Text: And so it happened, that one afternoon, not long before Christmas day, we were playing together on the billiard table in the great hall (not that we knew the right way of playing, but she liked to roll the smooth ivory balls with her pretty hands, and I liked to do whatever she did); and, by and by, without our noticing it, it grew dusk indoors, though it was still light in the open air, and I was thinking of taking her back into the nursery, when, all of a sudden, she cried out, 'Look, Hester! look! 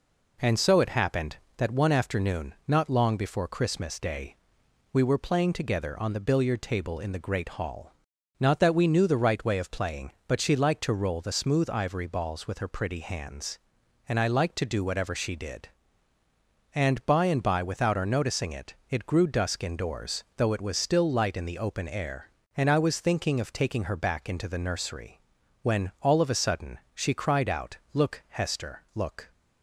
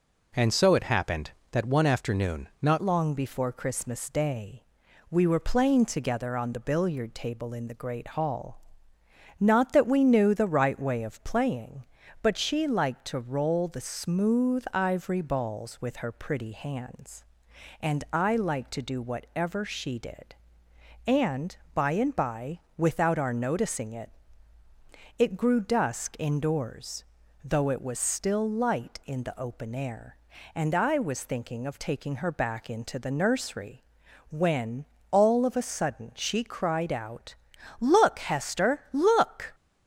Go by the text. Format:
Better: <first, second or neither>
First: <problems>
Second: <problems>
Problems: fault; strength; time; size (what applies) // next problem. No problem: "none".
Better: first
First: none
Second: changes voice at "long"; from 2.8 s on; 36.7 s long